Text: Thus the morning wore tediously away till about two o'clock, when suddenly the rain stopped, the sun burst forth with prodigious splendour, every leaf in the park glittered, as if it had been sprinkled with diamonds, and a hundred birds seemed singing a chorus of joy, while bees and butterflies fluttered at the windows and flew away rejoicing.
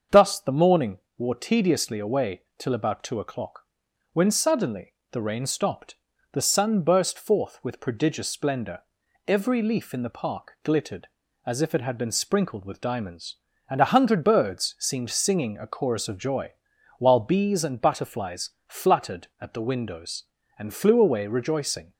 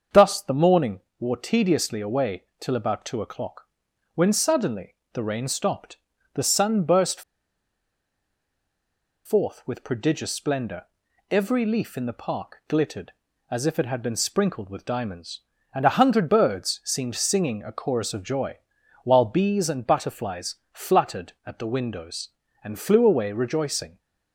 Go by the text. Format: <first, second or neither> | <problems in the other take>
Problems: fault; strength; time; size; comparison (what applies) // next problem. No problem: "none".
first | starts louder than the rest; until 1.3 s; 7 dB; also in the first // pauses between "morning" and "wore"; slight; at 1.0 s; 0.18 s long; slight in the first // pauses between "away" and "till"; slight; at 2.4 s; 0.16 s long; slight in the first // pauses between "suddenly" and "the"; slight; at 4.9 s; 0.18 s long; slight in the first // pauses between "burst" and "forth"; strong; at 7.2 s; 2.0 s long // pauses between "butterflies" and "fluttered"; slight; at 20.5 s; 0.16 s long; slight in the first